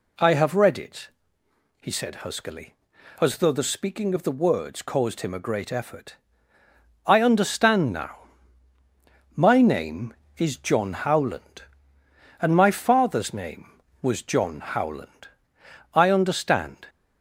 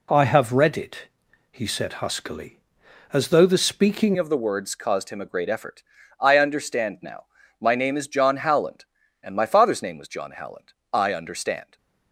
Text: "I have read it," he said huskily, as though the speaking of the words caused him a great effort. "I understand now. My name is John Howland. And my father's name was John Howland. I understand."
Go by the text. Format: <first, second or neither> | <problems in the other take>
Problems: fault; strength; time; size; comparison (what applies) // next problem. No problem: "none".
first | changes voice at "of"; from 4.1 s on; 7.6 s long